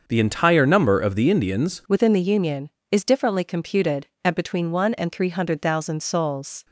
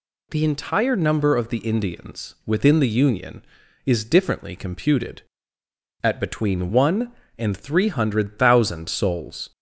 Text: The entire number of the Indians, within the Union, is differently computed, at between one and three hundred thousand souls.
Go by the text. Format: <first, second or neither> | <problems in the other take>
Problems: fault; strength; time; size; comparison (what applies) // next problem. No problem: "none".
second | starts louder than the rest; until 1.0 s; 6.5 dB // changes voice at "within"; from 1.8 s on; 4.8 s long